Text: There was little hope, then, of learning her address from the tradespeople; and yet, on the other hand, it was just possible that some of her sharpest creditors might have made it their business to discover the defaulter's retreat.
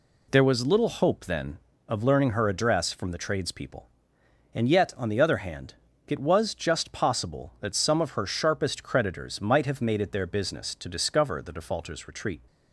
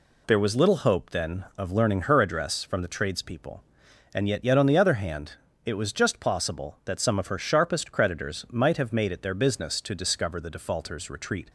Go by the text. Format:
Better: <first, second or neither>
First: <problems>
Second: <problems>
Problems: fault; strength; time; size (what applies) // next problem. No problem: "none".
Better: first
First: none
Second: says "yet" twice; at 4.4 s